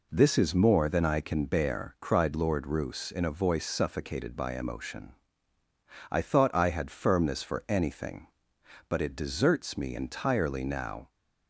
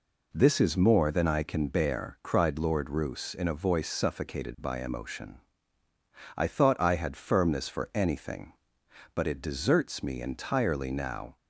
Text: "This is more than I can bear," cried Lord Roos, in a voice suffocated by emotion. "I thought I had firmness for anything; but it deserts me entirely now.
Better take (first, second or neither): neither